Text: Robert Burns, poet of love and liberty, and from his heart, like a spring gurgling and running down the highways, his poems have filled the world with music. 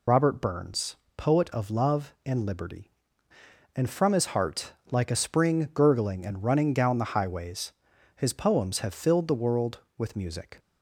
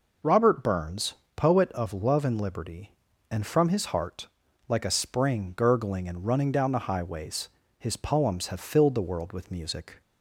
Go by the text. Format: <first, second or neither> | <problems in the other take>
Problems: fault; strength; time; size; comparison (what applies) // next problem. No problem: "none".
second | loses the start of "Robert"; at 0.0 s; 40 ms